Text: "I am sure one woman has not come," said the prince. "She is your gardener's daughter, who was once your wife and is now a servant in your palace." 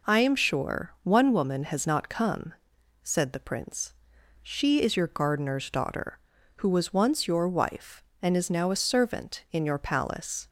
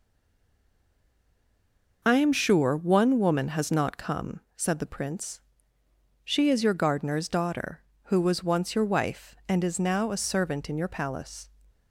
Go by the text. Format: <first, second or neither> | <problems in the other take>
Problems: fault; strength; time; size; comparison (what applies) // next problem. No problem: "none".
first | stays silent before the first word; noticeable; until 2.0 s; 2.0 s long